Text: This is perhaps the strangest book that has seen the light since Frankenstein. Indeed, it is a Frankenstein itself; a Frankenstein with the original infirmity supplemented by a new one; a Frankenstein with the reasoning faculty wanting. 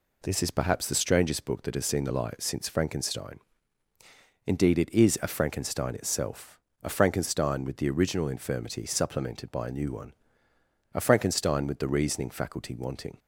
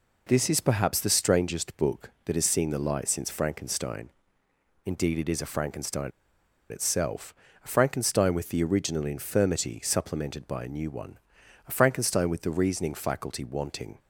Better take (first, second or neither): first